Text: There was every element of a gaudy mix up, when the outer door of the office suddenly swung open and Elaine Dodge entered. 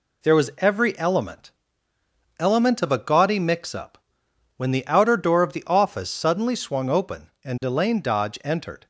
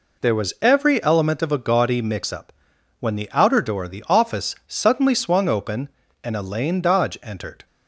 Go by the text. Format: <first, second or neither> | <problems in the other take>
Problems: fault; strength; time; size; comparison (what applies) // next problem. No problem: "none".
second | says "element" twice; at 2.3 s